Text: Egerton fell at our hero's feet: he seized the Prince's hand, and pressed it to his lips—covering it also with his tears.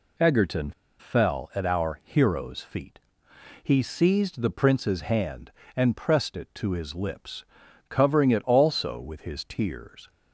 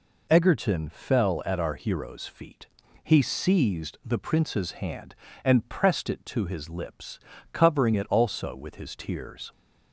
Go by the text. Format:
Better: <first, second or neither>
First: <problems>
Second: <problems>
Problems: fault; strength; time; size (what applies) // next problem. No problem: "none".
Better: second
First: pauses between "Egerton" and "fell"; slight; at 0.7 s; 0.28 s long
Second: none